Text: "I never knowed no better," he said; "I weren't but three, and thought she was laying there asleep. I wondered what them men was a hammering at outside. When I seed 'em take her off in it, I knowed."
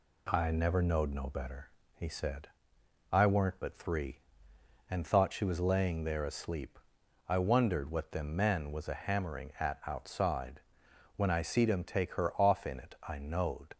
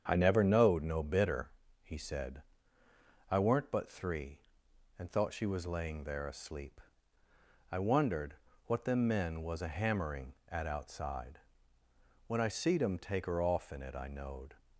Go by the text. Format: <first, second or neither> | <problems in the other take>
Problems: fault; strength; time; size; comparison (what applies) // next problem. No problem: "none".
first | starts louder than the rest; strong; until 1.0 s; 7.5 dB // says "bitter" for "better"; at 1.0 s // pauses between "wondered" and "what"; slight; at 8.3 s; 0.30 s long